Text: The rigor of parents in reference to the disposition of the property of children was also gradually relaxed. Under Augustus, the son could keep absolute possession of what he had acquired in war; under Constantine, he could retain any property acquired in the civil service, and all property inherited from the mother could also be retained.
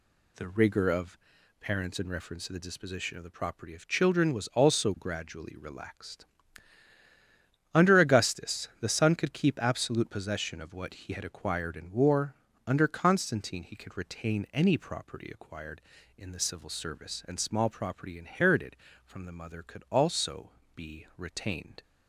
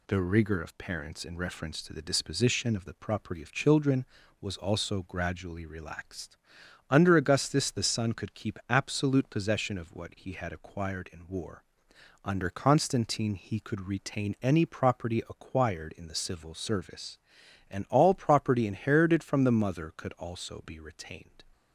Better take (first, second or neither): second